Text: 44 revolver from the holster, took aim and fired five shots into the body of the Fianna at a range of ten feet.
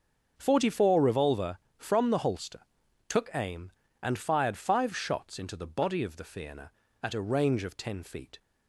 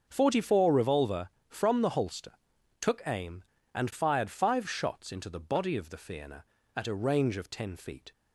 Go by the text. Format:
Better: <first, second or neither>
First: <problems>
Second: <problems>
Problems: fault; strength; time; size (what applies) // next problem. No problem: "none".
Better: neither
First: starts louder than the rest; until 1.3 s; 6.5 dB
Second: starts louder than the rest; until 1.1 s; 6.5 dB